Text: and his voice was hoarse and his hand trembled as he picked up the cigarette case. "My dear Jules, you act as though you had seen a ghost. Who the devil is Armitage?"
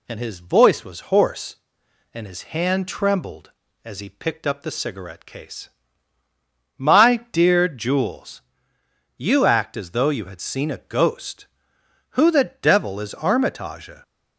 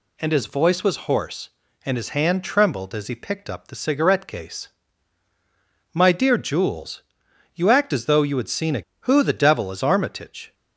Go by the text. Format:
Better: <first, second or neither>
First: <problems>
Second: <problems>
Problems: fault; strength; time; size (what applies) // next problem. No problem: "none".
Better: first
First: none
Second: skips "ghost"; at 8.9 s